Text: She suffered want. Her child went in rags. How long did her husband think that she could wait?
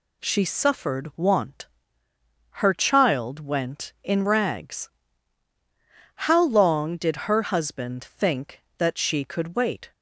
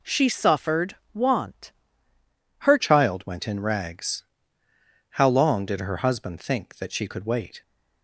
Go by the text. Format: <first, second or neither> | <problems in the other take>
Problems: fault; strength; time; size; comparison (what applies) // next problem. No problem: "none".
first | pauses between "suffered" and "want"; slight; at 0.9 s; 0.18 s long // changes voice at "child"; from 2.7 s on; 4.9 s long